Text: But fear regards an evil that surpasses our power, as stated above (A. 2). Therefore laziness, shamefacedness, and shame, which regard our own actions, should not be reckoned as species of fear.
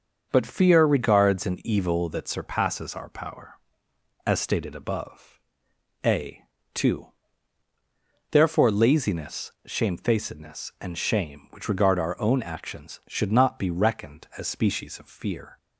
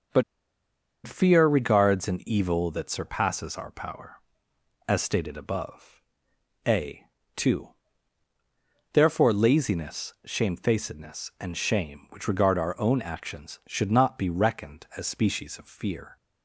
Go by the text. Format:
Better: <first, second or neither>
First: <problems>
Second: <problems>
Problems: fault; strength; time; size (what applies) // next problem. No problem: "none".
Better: first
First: starts louder than the rest; until 1.3 s; 6.5 dB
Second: starts louder than the rest; until 1.9 s; 6.5 dB // pauses between "But" and "fear"; noticeable; at 0.2 s; 0.82 s long